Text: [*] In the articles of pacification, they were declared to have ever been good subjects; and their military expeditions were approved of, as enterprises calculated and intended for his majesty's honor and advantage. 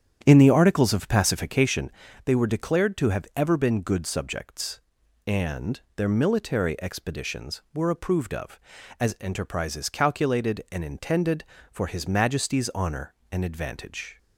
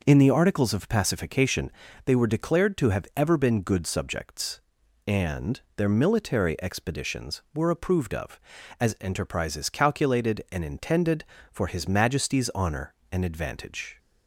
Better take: second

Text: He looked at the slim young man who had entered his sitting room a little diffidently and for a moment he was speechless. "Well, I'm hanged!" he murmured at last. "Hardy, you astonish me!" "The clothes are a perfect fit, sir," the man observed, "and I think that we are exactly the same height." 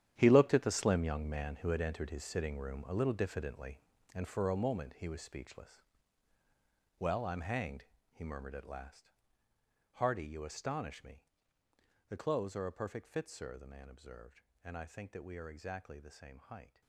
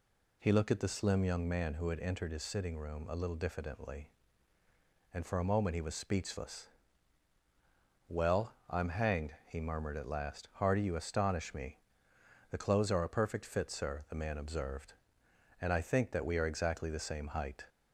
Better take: second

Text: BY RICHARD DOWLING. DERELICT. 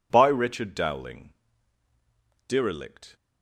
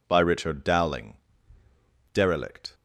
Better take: neither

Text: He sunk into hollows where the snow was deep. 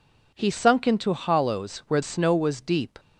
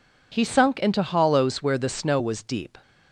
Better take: second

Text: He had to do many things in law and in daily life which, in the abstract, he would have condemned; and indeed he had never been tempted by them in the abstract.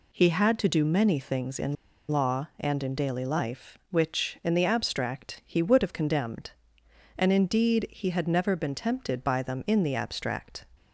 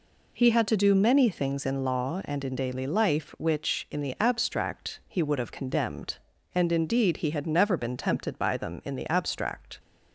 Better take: second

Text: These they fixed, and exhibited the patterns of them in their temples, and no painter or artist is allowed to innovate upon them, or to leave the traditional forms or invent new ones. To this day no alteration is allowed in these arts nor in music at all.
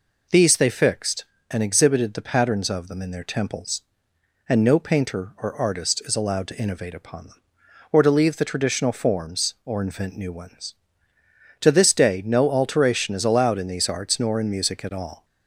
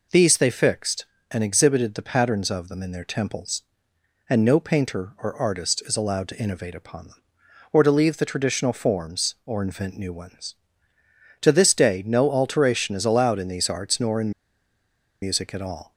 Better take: first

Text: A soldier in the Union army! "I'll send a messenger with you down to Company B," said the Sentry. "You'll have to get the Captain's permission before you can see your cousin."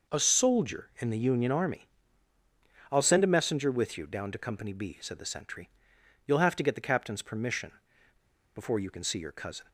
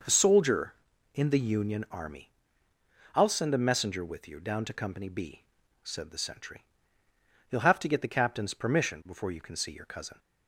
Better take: second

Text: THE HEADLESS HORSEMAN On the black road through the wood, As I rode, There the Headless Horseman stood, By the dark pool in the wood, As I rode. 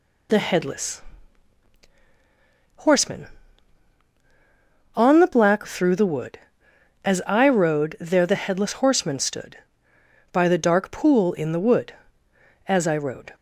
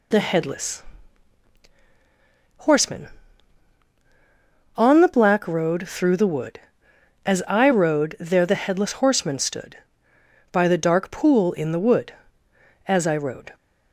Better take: second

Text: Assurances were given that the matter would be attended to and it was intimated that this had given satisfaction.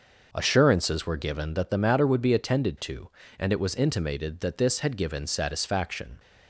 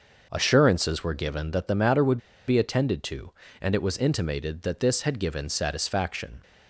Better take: first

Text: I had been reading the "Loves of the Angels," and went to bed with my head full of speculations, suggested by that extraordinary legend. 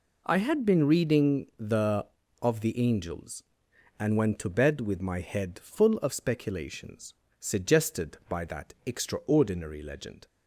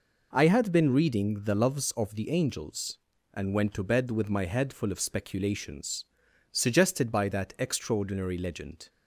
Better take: second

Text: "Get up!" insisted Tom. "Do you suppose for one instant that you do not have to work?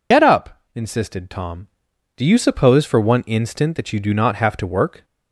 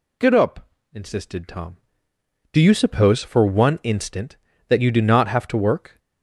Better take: second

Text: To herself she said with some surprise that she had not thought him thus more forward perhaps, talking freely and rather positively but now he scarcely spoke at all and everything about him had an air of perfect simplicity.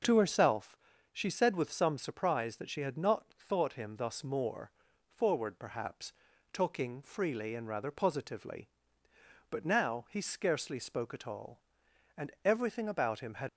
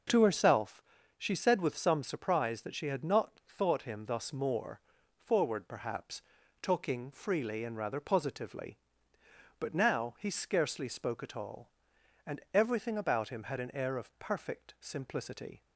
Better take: second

